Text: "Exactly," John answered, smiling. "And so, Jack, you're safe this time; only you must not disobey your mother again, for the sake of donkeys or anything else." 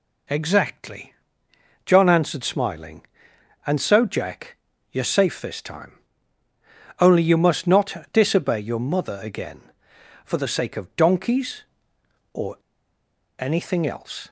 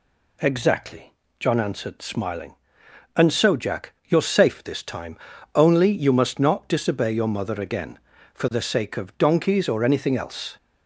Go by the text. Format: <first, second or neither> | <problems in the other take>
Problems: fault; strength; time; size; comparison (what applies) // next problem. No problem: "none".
second | pauses between "or" and "anything"; noticeable; at 12.5 s; 0.80 s long